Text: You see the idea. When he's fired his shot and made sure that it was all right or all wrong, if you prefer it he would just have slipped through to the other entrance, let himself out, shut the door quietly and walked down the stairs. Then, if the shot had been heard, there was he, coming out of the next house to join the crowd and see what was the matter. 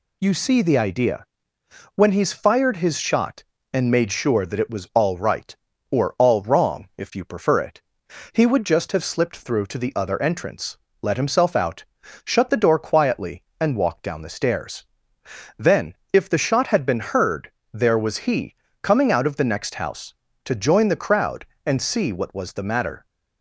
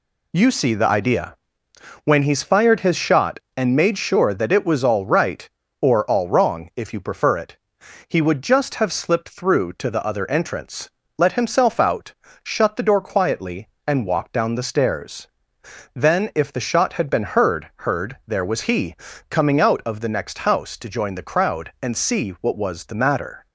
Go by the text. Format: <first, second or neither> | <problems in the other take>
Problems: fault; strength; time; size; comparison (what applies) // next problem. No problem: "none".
first | pauses between "it" and "he"; noticeable; at 7.5 s; 0.50 s long; noticeable in the first // says "heard" twice; at 17.7 s